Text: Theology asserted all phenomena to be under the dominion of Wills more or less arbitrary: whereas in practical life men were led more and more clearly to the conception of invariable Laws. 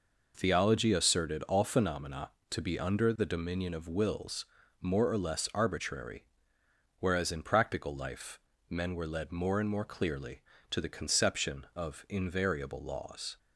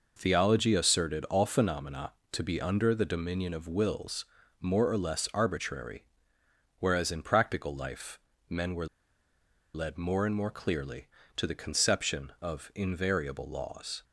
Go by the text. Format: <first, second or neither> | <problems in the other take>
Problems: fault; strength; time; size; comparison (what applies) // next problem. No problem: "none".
first | pauses between "Wills" and "more"; slight; at 4.2 s; 0.34 s long; slight in the first // pauses between "life" and "men"; slight; at 8.1 s; 0.32 s long; slight in the first // pauses between "were" and "led"; noticeable; at 8.8 s; 0.87 s long